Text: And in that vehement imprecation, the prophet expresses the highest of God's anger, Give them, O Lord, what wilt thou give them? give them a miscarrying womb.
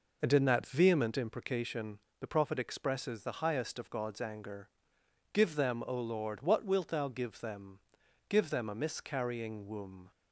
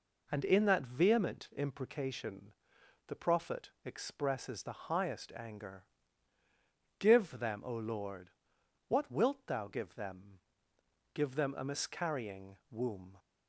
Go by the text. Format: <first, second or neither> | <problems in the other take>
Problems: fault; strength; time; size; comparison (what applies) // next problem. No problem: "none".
first | pauses between "prophet" and "expresses"; slight; at 3.6 s; 0.16 s long // skips "of God's"; at 5.3 s